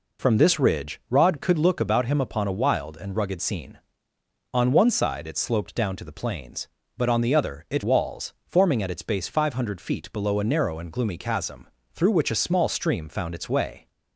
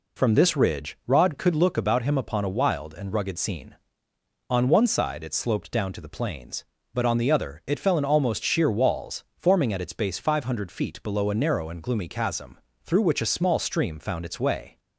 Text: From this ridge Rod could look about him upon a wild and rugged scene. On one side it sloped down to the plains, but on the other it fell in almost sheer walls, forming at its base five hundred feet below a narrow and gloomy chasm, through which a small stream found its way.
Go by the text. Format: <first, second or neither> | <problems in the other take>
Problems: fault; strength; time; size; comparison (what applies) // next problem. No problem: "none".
second | skips "fell in almost sheer"; at 7.8 s